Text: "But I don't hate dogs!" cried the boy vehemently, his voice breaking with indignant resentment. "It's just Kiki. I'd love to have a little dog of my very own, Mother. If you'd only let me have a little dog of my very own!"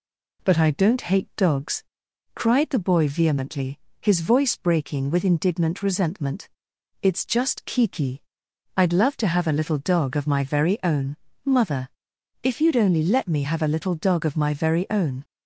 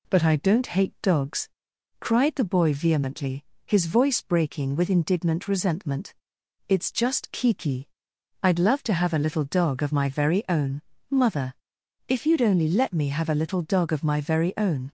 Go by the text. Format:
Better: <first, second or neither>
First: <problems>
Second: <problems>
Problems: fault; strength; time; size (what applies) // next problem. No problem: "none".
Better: neither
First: none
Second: none